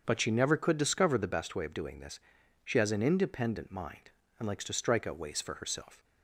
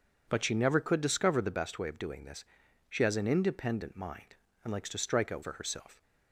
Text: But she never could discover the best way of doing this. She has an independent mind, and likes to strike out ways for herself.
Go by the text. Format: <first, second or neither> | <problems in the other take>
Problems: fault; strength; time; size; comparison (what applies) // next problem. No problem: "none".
first | starts louder than the rest; until 1.2 s; 7 dB; strong in the first // skips "ways"; at 5.4 s